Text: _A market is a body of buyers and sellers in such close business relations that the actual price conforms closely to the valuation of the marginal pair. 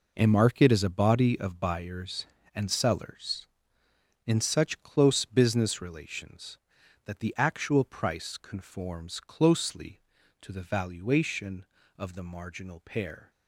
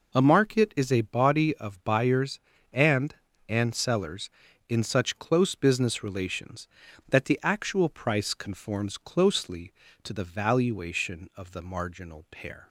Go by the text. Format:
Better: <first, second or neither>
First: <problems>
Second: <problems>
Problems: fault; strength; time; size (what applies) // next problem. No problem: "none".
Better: first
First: none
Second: says "and" twice; at 3.4 s